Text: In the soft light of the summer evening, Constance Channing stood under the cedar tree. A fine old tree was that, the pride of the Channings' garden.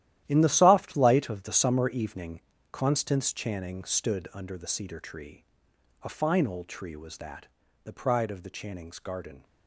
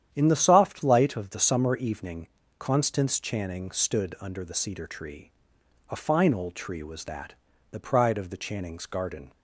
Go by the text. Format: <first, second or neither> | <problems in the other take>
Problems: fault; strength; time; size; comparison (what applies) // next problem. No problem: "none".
second | gets quieter; strong; throughout; 12.5 dB // starts louder than the rest; strong; until 1.2 s; 12.5 dB; strong in the second